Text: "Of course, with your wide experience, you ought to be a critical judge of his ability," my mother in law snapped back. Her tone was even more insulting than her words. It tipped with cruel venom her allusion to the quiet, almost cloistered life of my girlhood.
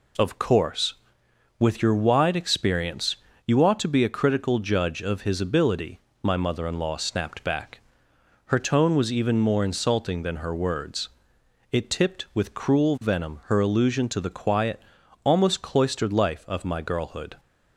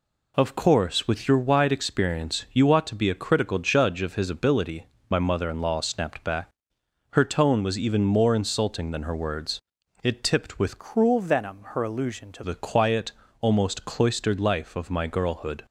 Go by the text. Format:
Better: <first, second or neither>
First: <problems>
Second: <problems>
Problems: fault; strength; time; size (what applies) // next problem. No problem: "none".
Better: first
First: none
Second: changes voice from "cruel" to "to"; from 10.7 to 12.4 s; 1.7 s long